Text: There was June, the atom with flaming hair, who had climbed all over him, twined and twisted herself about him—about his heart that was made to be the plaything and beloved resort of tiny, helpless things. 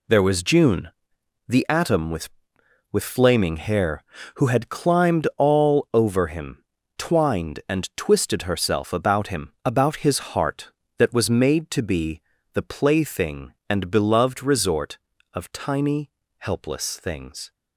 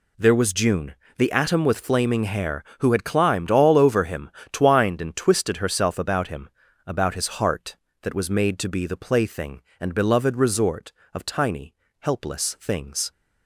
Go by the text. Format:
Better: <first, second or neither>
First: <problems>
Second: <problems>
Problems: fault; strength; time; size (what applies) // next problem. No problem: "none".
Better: second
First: says "with" twice; at 2.9 s // pauses between "be" and "the"; slight; at 12.2 s; 0.32 s long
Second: none